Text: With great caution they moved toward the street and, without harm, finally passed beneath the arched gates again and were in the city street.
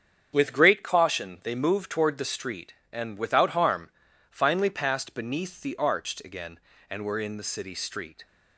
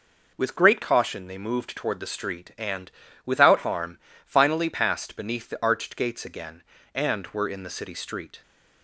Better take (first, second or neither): second